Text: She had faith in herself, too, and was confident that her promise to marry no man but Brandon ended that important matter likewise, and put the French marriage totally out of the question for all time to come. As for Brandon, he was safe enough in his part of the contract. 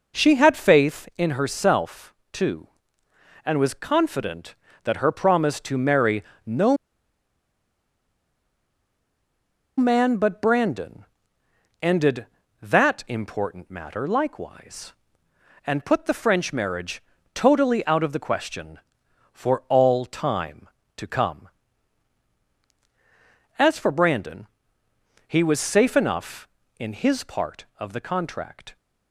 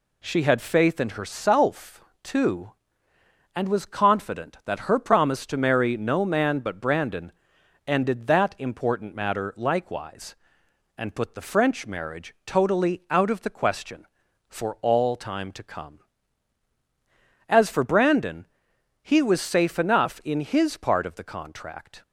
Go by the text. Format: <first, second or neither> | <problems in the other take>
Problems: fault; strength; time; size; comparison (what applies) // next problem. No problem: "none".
second | pauses between "marry" and "no"; slight; at 6.2 s; 0.24 s long // pauses between "no" and "man"; strong; at 6.7 s; 3.0 s long // pauses between "Brandon" and "ended"; noticeable; at 11.0 s; 0.76 s long; noticeable in the second // pauses between "marriage" and "totally"; slight; at 17.0 s; 0.32 s long